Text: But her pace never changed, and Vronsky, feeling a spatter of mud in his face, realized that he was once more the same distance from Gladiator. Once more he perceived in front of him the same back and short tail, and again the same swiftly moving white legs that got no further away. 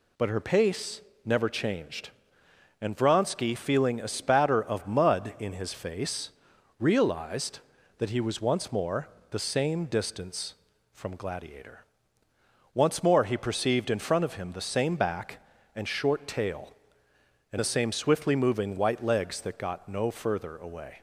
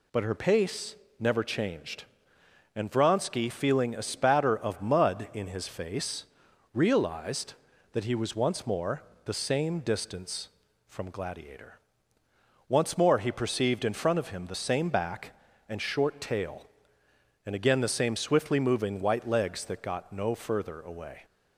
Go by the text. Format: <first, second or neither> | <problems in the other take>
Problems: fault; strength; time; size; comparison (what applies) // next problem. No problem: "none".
second | pauses between "pace" and "never"; slight; at 1.0 s; 0.24 s long; slight in the second // pauses between "more" and "the"; slight; at 9.0 s; 0.24 s long; slight in the second // skips "again"; at 17.5 s